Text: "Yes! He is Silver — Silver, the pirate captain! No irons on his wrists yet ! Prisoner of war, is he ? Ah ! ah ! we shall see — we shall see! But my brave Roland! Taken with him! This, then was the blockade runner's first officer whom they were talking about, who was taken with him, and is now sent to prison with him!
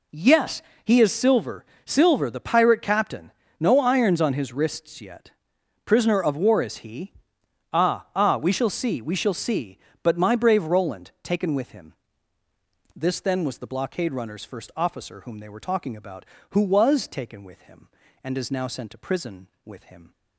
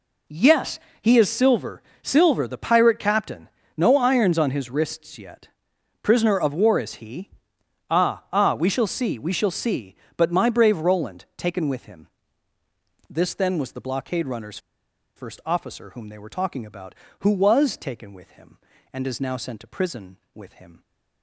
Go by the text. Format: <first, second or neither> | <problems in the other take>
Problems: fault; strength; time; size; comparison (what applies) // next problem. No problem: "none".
first | pauses between "runner's" and "first"; noticeable; at 14.5 s; 0.57 s long